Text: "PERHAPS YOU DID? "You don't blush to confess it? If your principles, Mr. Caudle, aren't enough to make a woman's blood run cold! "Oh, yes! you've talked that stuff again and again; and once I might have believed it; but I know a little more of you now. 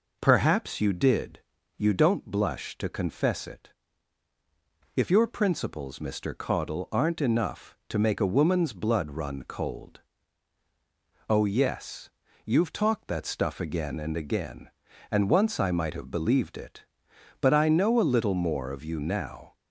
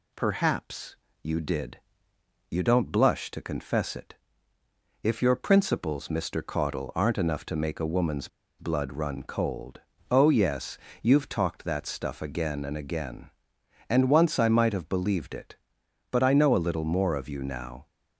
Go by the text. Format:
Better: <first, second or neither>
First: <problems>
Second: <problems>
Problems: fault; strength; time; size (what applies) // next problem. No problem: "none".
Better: first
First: none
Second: pauses between "PERHAPS" and "YOU"; slight; at 0.9 s; 0.28 s long // pauses between "woman's" and "blood"; slight; at 8.2 s; 0.31 s long